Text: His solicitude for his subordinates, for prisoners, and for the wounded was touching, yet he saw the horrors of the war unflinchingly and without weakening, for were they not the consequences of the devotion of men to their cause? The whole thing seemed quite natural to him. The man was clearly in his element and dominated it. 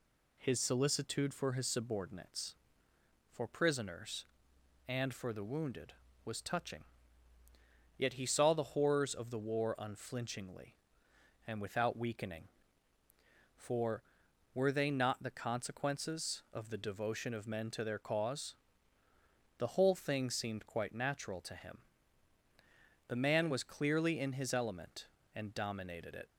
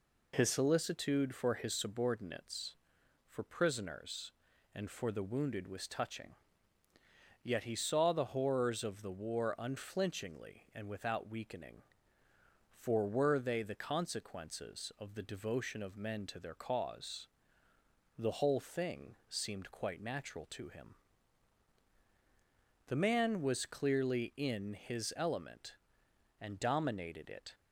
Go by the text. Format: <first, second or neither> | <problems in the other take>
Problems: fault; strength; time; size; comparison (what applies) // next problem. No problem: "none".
first | skips "not"; at 13.6 s